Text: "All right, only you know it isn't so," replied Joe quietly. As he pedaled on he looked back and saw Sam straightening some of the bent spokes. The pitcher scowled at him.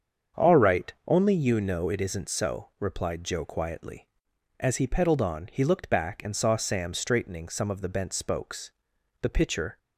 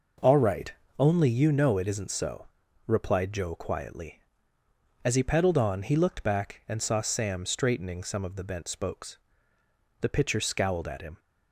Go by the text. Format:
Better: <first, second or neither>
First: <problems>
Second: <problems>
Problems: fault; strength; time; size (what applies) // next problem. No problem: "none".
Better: second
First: starts louder than the rest; strong; until 1.5 s; 7.5 dB // stops before "scowled at him"; at 9.7 s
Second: none